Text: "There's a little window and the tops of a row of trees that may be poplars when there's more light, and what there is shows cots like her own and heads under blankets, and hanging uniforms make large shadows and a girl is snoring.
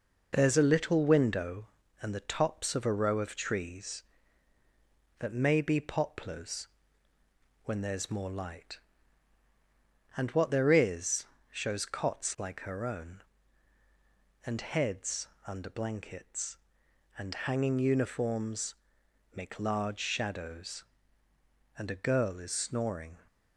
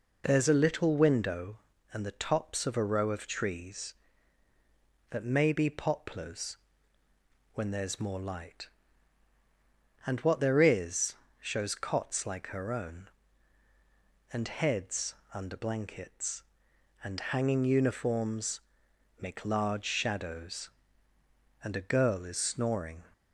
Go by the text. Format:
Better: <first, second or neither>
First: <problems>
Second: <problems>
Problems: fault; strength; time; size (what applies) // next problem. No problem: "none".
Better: second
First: gets quieter; throughout; 3.5 dB // pauses between "poplars" and "when"; at 6.6 s; 1.0 s long // pauses between "is" and "shows"; slight; at 11.2 s; 0.26 s long // pauses between "heads" and "under"; slight; at 15.2 s; 0.20 s long // pauses between "uniforms" and "make"; noticeable; at 18.7 s; 0.60 s long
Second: pauses between "poplars" and "when"; at 6.5 s; 1.0 s long // pauses between "is" and "shows"; slight; at 11.1 s; 0.26 s long // pauses between "heads" and "under"; slight; at 15.1 s; 0.20 s long // pauses between "uniforms" and "make"; noticeable; at 18.6 s; 0.60 s long